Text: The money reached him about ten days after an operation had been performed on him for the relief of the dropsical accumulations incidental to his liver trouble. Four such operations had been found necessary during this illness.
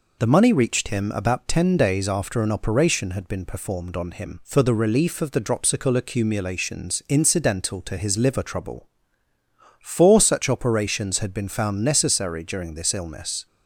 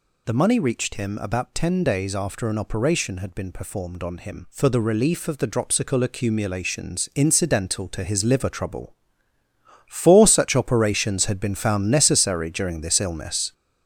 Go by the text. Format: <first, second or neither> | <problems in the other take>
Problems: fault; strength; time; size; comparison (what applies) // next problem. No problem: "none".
first | gets louder; throughout; 6 dB